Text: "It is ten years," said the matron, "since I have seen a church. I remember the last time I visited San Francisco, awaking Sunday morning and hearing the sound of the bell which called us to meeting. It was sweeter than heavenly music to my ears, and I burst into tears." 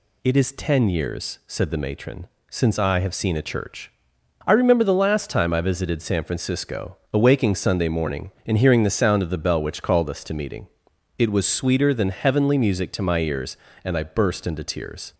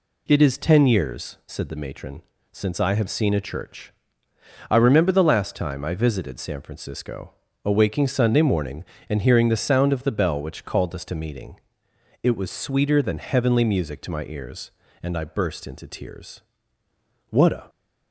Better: first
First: none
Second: goes on to say "What a"; slight; from 17.2 s on; 0.40 s long

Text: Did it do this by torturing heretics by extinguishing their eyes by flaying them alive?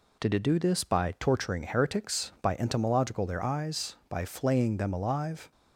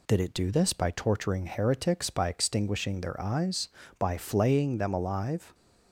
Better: second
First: says "entomological" for "extinguishing"; at 2.5 s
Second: none

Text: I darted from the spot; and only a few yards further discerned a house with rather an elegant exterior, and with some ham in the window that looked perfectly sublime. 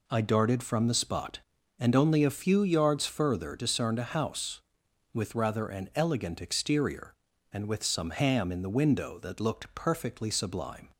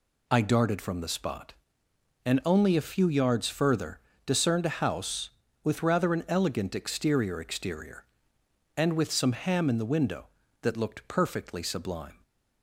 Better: first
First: none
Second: pauses between "further" and "discerned"; slight; at 4.0 s; 0.26 s long // says "exterior" twice; at 7.4 s

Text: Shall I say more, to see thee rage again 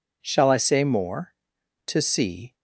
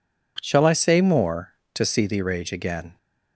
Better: second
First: stops before "thee rage again"; at 2.5 s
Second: none

